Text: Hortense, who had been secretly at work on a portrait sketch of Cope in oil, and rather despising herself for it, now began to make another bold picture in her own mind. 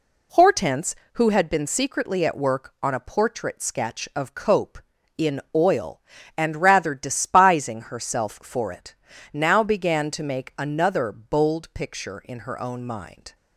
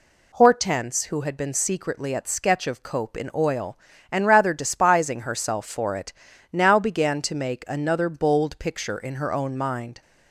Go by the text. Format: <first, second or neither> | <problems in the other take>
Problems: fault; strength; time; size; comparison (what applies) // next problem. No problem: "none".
first | skips "work on a portrait"; at 2.2 s